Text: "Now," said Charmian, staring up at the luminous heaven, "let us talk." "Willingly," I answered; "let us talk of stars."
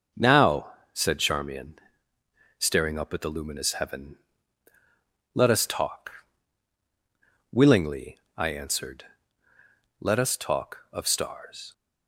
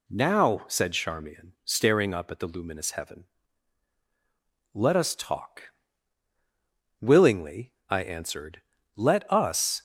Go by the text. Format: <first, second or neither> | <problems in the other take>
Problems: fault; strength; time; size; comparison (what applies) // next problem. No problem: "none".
first | stops before "talk of stars"; at 9.7 s